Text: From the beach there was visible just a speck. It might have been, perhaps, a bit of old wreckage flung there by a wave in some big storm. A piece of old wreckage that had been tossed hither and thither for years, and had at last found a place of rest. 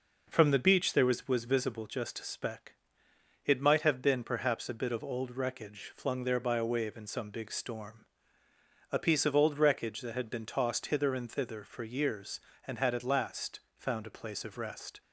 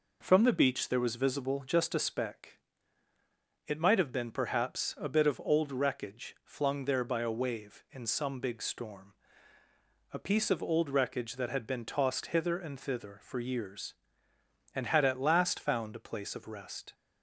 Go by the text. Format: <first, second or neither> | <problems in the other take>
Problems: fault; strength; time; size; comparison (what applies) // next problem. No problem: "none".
second | says "was" twice; at 1.2 s // pauses between "last" and "found"; slight; at 13.5 s; 0.20 s long